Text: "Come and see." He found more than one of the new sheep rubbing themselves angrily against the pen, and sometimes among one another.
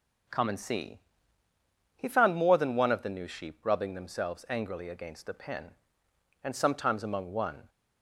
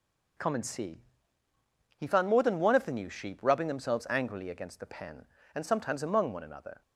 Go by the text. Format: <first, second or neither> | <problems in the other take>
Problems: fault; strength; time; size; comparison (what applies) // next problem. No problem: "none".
second | stops before "another"; at 7.6 s